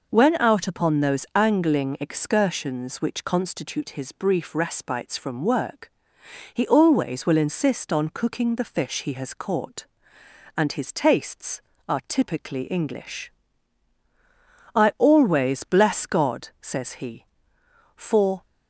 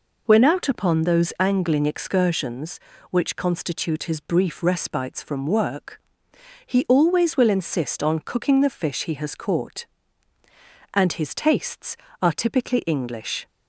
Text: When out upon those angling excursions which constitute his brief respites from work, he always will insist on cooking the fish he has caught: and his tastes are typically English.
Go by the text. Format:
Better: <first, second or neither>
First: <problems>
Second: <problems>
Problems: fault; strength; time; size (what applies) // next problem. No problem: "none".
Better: second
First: goes on to say "I always bless God says he for"; strong; from 14.7 s on; 3.7 s long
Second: none